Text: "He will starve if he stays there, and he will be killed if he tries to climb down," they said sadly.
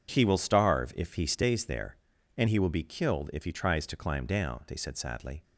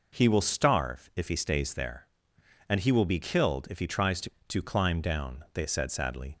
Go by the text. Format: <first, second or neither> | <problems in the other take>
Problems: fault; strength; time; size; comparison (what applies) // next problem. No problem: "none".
first | says "to" twice; at 4.4 s